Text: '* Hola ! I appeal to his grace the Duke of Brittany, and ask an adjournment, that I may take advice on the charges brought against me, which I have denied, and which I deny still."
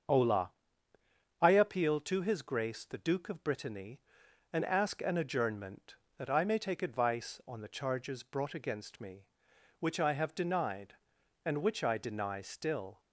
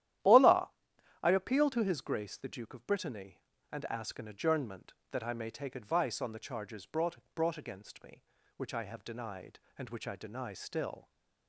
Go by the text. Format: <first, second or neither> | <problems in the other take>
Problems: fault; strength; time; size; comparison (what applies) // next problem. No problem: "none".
first | starts louder than the rest; strong; until 1.7 s; 12 dB; also in the first // says "brought" twice; at 7.3 s